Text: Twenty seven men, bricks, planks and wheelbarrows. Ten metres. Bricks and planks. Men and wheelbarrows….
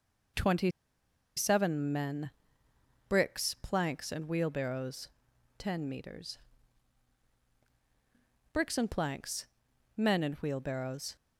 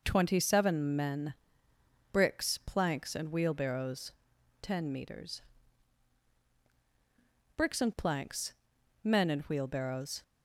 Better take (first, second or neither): second